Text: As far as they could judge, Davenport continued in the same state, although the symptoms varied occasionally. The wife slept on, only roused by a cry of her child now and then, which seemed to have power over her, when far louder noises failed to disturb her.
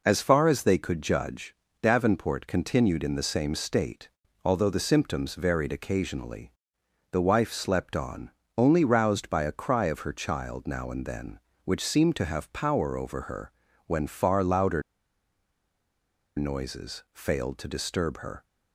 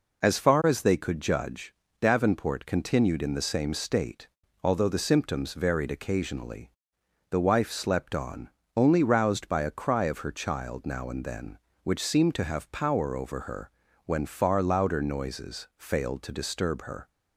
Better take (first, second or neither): second